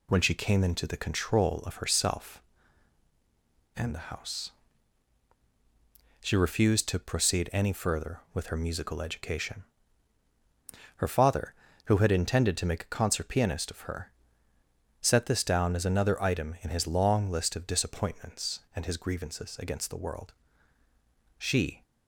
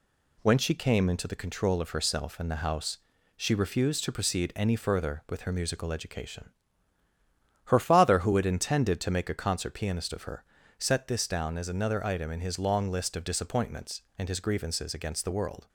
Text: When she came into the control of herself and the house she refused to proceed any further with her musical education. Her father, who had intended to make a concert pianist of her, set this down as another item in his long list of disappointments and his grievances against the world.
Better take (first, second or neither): second